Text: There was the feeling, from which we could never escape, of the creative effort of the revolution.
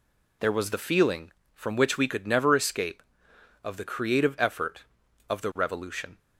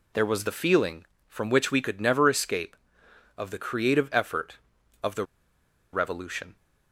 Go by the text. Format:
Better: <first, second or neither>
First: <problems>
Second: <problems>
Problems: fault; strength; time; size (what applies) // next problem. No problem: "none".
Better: first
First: none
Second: pauses between "the" and "revolution"; noticeable; at 5.2 s; 0.68 s long